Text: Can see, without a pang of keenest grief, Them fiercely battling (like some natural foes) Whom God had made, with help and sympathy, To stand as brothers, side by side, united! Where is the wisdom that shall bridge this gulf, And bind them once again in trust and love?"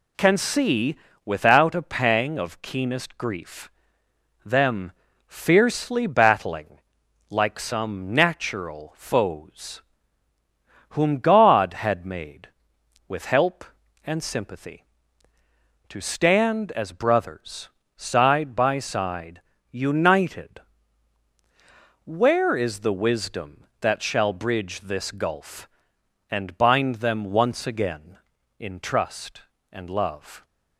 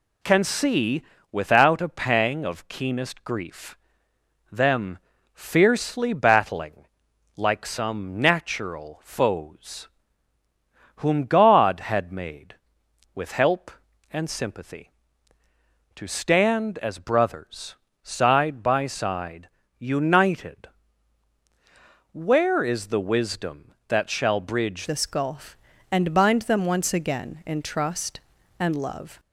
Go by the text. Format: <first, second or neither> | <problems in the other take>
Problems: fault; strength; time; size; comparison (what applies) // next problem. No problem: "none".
first | pauses between "Them" and "fiercely"; slight; at 4.9 s; 0.36 s long; slight in the first // changes voice at "this"; from 24.8 s on; 4.3 s long